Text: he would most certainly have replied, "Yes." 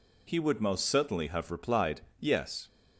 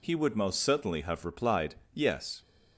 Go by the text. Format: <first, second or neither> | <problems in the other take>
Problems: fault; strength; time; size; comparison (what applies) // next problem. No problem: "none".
neither | none